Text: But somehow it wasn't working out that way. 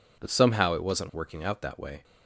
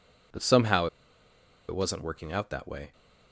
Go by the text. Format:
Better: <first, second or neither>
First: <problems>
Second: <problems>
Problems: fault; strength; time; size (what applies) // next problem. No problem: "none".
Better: first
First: none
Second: pauses between "somehow" and "it"; noticeable; at 0.8 s; 0.82 s long